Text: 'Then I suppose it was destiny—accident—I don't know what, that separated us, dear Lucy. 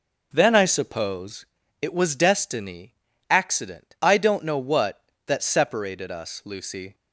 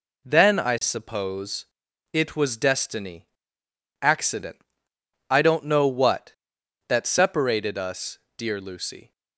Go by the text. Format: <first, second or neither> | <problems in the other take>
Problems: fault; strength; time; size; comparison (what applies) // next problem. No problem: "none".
second | pauses between "suppose" and "it"; at 1.4 s; 0.37 s long; noticeable in the second // skips "dear"; at 6.4 s